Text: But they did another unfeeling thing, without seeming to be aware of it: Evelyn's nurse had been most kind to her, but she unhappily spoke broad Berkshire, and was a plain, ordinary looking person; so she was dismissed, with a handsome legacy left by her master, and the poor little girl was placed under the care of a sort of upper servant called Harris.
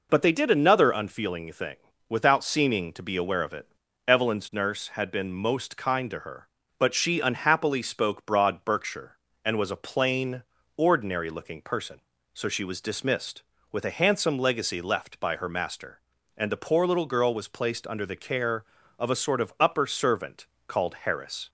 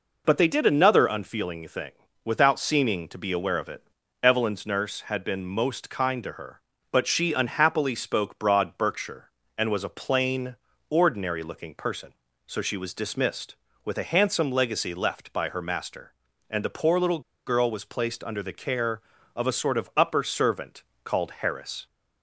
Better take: first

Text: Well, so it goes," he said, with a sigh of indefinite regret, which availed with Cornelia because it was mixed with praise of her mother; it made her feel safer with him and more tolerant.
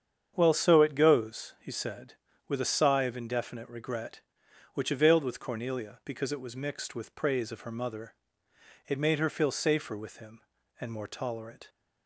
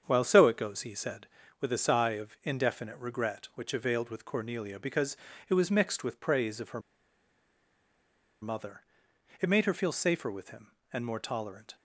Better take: first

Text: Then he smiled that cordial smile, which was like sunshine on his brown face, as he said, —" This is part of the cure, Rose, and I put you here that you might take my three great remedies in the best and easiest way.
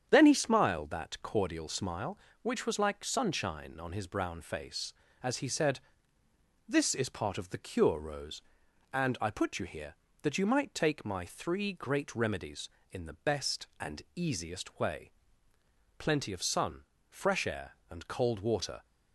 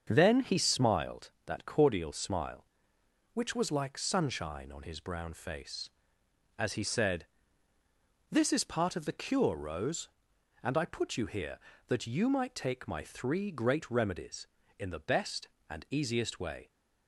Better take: second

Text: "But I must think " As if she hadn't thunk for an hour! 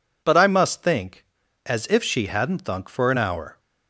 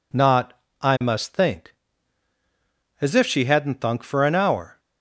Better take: first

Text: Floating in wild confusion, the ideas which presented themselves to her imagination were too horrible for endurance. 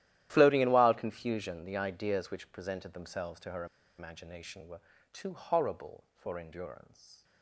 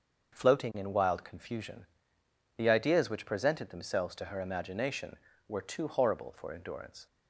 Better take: second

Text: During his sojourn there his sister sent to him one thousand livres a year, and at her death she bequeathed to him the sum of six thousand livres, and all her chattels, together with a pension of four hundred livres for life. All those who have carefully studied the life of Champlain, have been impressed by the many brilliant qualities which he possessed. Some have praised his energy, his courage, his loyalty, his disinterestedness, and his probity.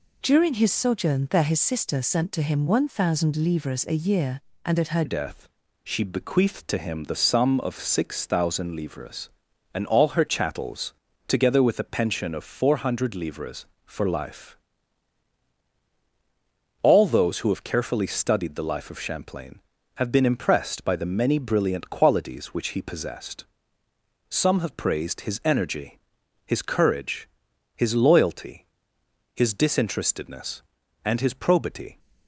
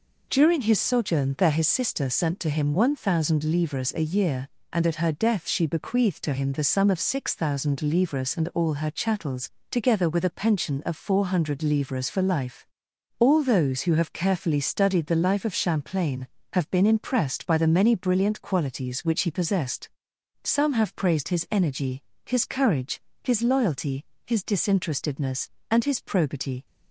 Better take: second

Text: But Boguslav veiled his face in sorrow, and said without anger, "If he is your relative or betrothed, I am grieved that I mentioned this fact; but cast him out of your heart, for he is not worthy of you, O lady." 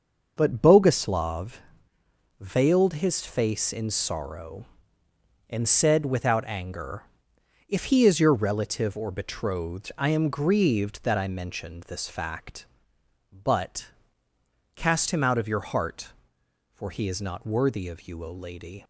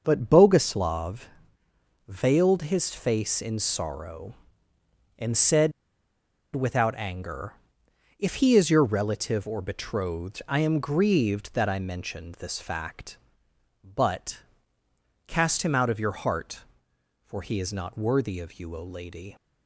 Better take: first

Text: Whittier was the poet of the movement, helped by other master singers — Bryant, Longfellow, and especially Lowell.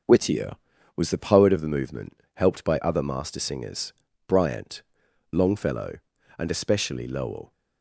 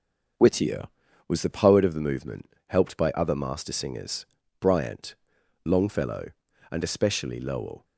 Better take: neither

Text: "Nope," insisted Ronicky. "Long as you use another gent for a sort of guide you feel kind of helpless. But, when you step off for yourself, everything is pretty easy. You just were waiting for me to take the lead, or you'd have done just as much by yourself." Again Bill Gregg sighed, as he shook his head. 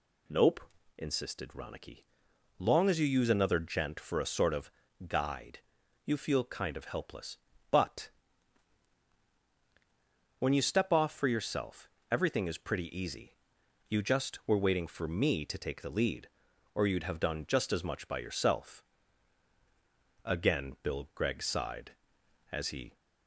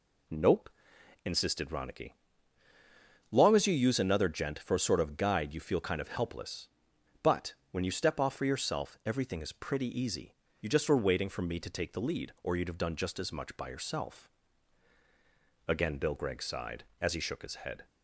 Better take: second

